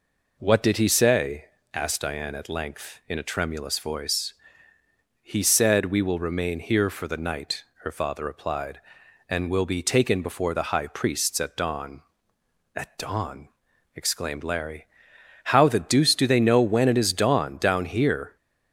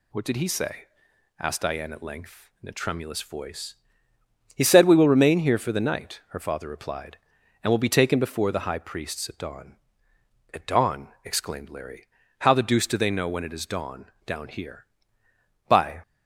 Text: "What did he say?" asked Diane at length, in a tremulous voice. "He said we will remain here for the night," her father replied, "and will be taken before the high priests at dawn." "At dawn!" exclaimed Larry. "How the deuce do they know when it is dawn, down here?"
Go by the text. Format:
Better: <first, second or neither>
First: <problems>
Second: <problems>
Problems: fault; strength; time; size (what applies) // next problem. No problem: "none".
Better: first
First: none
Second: goes on to say "By"; slight; from 15.6 s on; 0.32 s long